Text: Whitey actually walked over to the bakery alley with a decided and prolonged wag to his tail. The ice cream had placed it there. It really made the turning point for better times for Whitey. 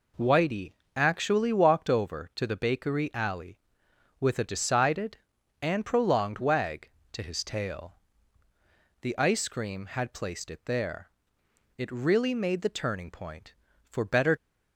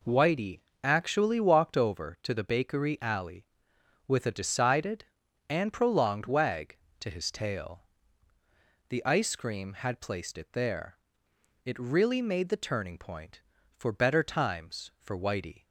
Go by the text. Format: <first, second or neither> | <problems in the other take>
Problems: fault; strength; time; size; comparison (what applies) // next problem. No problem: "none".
second | pauses between "Whitey" and "actually"; slight; at 0.7 s; 0.22 s long; slight in the second // stops before "times for Whitey"; at 14.3 s